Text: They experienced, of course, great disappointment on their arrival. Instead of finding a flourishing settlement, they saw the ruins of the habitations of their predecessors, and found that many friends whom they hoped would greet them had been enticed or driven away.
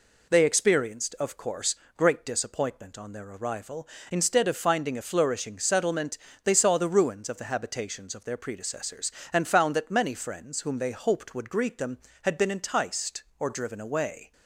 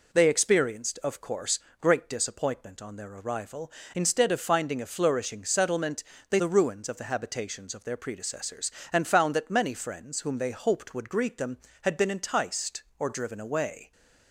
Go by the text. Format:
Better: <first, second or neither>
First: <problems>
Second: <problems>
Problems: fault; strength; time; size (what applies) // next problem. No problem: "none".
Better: first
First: none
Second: skips "saw"; at 6.3 s